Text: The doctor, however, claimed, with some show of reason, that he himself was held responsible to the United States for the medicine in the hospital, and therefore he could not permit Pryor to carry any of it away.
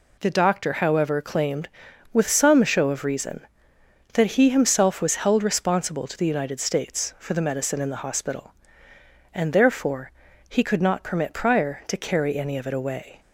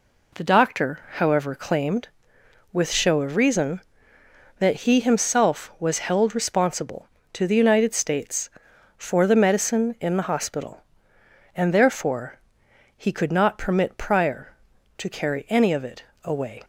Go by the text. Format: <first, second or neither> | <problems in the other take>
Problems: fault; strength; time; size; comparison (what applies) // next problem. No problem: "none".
first | skips "some"; at 2.8 s // pauses between "therefore" and "he"; noticeable; at 12.3 s; 0.58 s long; slight in the first // pauses between "it" and "away"; slight; at 16.0 s; 0.20 s long